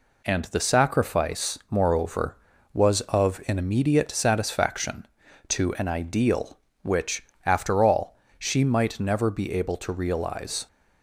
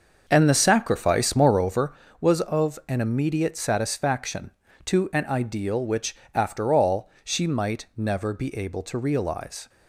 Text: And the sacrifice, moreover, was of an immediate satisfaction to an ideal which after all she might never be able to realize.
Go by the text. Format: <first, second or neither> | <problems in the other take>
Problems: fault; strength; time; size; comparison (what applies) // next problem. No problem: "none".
first | starts louder than the rest; until 1.8 s; 6.5 dB // pauses between "which" and "after"; slight; at 6.1 s; 0.18 s long; slight in the first // pauses between "all" and "she"; slight; at 7.0 s; 0.16 s long; slight in the first